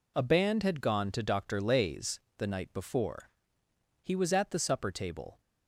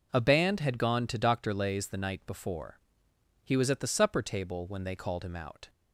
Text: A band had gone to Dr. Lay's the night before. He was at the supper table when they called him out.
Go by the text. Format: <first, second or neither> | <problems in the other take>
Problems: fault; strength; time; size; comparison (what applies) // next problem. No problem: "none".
second | pauses between "Lay's" and "the"; slight; at 2.1 s; 0.20 s long // stops before "when they called him out"; at 5.3 s